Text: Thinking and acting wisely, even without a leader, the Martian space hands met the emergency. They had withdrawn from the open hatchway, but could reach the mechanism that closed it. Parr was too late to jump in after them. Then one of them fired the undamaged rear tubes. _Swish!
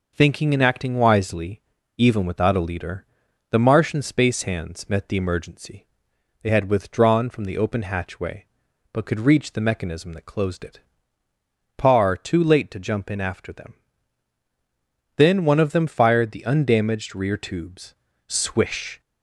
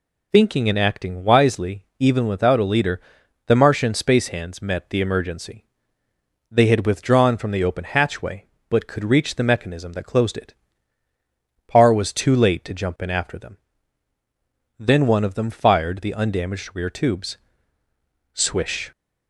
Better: second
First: skips "was"; at 12.1 s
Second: none

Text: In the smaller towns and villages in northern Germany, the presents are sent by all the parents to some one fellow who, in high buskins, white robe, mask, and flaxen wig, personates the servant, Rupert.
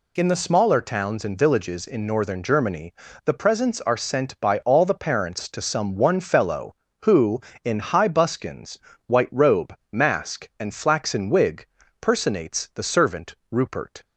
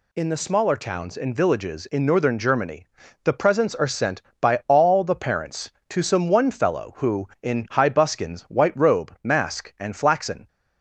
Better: first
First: none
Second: stops before "wig personates the servant Rupert"; at 10.4 s

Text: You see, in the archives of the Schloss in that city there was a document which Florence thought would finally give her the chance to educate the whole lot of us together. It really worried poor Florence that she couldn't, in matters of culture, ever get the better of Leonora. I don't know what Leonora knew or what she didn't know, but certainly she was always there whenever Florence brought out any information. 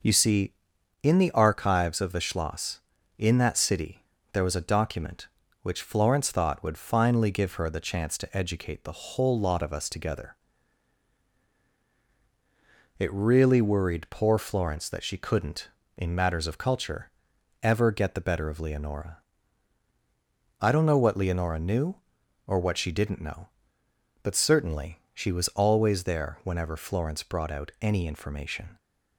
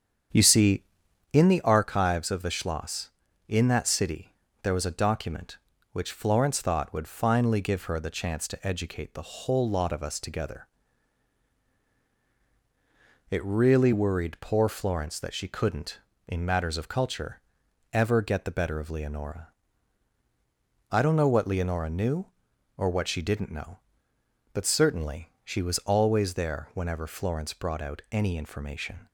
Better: first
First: pauses between "city" and "there"; slight; at 4.0 s; 0.30 s long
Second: starts louder than the rest; strong; until 1.6 s; 8 dB // pauses between "city" and "there"; slight; at 4.3 s; 0.30 s long

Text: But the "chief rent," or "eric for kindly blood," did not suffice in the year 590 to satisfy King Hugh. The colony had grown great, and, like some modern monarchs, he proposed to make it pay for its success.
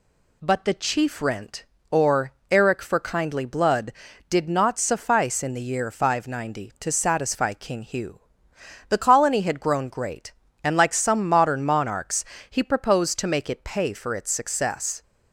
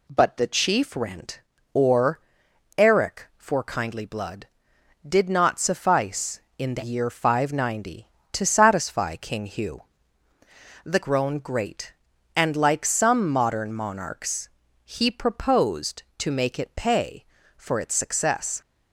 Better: first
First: pauses between "or" and "eric"; slight; at 2.3 s; 0.18 s long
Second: pauses between "or" and "eric"; noticeable; at 2.2 s; 0.58 s long // skips "colony had"; at 11.0 s

